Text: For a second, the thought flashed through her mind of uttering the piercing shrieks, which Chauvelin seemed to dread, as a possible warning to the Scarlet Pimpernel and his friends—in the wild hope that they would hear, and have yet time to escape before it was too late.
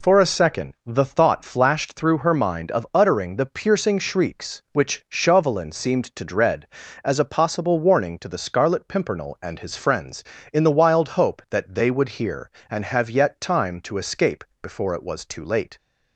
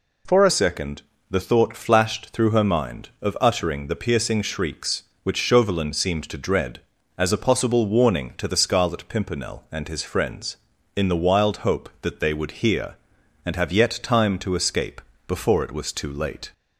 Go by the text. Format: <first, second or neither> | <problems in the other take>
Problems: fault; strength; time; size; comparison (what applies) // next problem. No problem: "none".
first | changes voice at "second"; from 0.4 s on; 16.1 s long // pauses between "escape" and "before"; slight; at 15.0 s; 0.26 s long; slight in the first